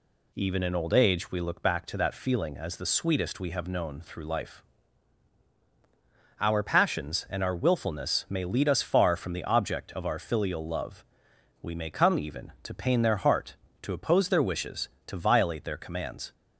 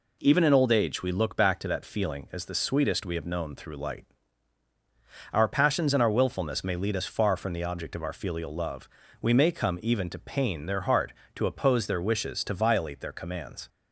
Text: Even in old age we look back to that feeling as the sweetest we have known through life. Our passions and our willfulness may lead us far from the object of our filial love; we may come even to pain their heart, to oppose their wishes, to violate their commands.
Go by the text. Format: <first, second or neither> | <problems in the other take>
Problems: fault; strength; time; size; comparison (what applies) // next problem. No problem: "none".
first | says "light" for "life"; at 3.7 s